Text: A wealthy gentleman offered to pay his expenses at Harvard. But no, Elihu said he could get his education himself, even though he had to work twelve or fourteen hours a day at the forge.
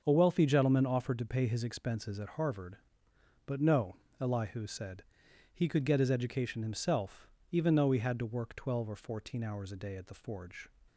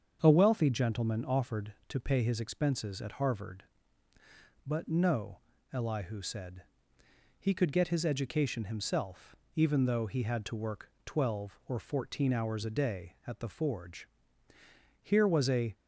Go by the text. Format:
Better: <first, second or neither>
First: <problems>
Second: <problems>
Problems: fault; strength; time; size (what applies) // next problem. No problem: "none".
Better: first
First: starts louder than the rest; until 1.0 s; 6.5 dB // pauses between "said" and "he"; noticeable; at 5.0 s; 0.50 s long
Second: starts louder than the rest; until 1.2 s; 7 dB // pauses between "said" and "he"; noticeable; at 6.6 s; 0.76 s long // pauses between "work" and "twelve"; slight; at 10.9 s; 0.16 s long // goes on to say "Here was a"; noticeable; from 15.0 s on; 0.72 s long